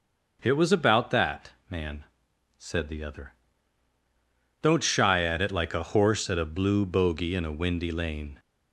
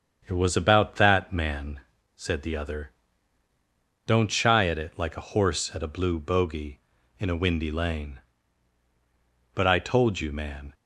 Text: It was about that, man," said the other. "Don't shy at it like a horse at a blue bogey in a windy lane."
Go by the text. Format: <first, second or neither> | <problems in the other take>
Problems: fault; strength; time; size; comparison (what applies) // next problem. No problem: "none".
first | starts louder than the rest; strong; until 1.2 s; 7.5 dB; noticeable in the first // goes on to say "But I told you man"; noticeable; from 9.5 s on; 1.2 s long